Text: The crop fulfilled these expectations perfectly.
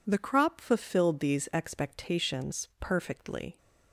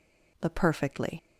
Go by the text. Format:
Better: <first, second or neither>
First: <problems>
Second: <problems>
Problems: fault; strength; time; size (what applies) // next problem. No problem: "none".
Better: first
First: none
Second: skips "crop fulfilled these expectations"; at 0.5 s